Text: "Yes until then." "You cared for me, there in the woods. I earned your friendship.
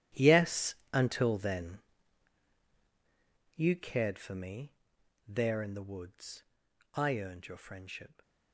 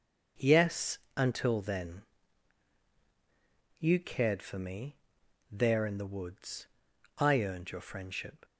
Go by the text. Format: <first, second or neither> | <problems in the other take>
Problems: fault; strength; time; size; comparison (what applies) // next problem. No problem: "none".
second | gets quieter; strong; throughout; 15.5 dB // starts louder than the rest; strong; until 1.3 s; 12.5 dB; also in the second // pauses between "Yes" and "until"; slight; at 0.7 s; 0.18 s long; slight in the second